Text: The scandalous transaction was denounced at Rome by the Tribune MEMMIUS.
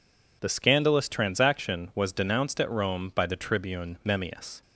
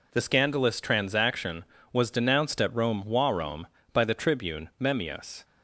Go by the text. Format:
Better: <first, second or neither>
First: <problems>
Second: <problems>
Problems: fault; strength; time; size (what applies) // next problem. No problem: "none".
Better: first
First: none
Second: says "Rome" twice; at 3.0 s